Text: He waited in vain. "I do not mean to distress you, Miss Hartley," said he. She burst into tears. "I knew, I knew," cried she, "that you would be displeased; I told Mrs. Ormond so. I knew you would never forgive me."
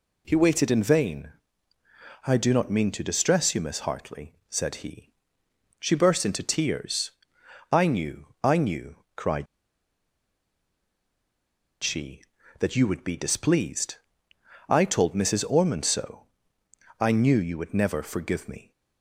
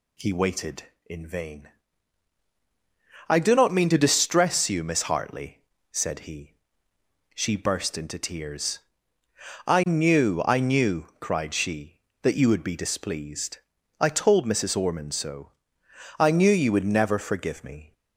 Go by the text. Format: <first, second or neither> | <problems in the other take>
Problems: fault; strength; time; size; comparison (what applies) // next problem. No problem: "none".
second | pauses between "cried" and "she"; strong; at 9.4 s; 2.3 s long